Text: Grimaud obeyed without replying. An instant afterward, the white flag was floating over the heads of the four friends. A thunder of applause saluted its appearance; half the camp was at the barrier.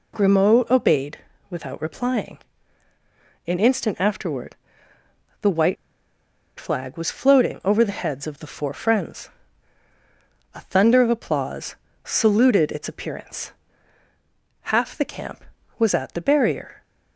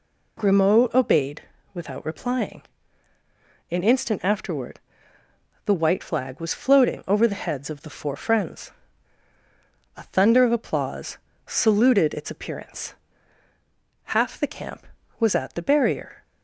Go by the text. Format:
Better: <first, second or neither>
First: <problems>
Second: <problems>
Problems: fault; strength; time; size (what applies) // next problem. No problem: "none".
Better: second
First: pauses between "obeyed" and "without"; slight; at 1.1 s; 0.32 s long // pauses between "white" and "flag"; noticeable; at 5.7 s; 0.81 s long // pauses between "applause" and "saluted"; slight; at 11.7 s; 0.30 s long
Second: pauses between "obeyed" and "without"; slight; at 1.4 s; 0.32 s long // pauses between "applause" and "saluted"; slight; at 11.1 s; 0.30 s long